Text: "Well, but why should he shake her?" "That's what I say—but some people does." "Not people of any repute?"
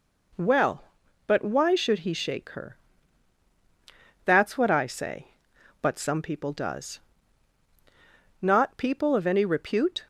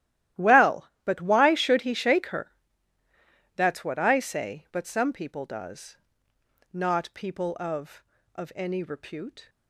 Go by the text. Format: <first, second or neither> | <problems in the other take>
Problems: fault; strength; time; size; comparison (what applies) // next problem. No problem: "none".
first | starts louder than the rest; strong; until 1.5 s; 13.5 dB // says "of" twice; at 8.3 s